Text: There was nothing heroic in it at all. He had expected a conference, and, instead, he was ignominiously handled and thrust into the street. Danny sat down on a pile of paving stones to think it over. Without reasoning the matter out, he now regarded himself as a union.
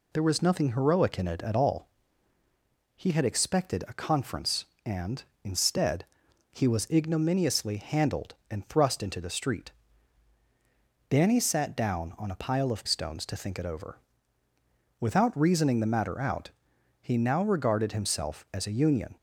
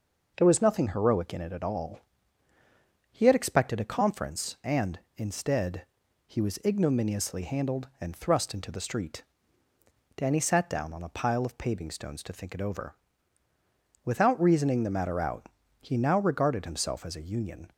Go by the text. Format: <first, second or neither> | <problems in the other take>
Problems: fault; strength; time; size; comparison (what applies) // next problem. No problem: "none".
second | skips "paving"; at 12.8 s